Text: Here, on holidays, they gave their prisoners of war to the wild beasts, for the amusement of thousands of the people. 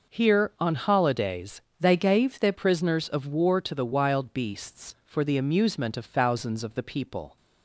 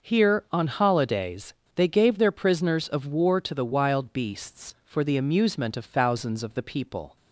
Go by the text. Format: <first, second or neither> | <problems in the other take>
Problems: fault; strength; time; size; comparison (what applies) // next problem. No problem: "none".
second | changes voice from "they" to "their"; from 1.7 to 2.5 s; 0.8 s long